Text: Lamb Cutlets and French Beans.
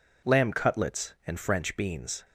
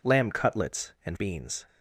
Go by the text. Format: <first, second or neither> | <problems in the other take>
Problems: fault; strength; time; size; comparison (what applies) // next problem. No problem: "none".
first | skips "French"; at 1.1 s